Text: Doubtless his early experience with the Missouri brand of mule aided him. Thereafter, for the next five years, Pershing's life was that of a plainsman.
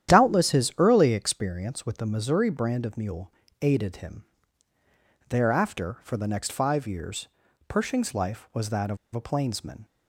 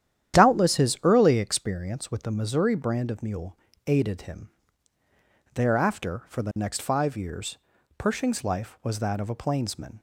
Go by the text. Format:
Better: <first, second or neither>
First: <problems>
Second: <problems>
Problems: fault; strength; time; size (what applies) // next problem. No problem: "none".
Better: second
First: starts louder than the rest; strong; until 1.1 s; 10.5 dB // pauses between "mule" and "aided"; slight; at 3.3 s; 0.30 s long // pauses between "of" and "a"; slight; at 8.9 s; 0.17 s long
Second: starts louder than the rest; strong; until 1.4 s; 10.5 dB // pauses between "mule" and "aided"; slight; at 3.5 s; 0.30 s long